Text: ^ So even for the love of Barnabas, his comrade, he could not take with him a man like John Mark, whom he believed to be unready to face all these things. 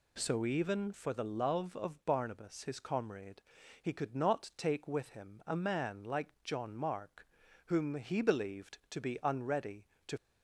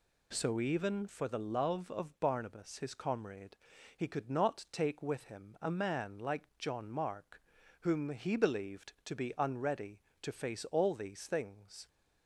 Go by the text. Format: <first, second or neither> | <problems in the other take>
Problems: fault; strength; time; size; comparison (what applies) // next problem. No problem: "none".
second | stops before "face all these things"; at 10.1 s